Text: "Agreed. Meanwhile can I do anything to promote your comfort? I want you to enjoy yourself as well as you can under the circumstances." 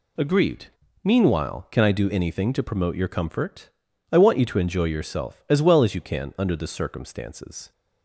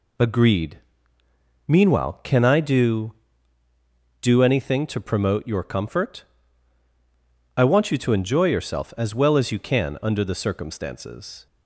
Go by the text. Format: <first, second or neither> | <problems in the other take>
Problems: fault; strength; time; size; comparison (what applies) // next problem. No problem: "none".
first | says "do" twice; at 4.2 s